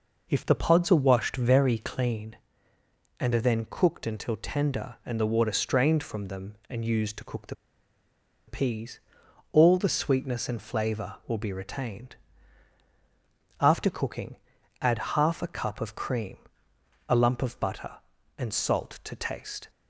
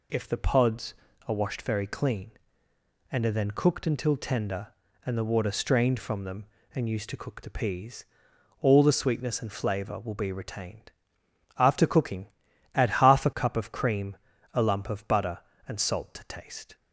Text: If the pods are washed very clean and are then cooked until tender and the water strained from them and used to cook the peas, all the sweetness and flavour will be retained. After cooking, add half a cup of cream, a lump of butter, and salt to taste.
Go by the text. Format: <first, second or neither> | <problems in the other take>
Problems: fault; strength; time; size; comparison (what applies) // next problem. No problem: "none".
second | pauses between "the" and "peas"; noticeable; at 7.5 s; 0.92 s long // pauses between "add" and "half"; slight; at 14.9 s; 0.16 s long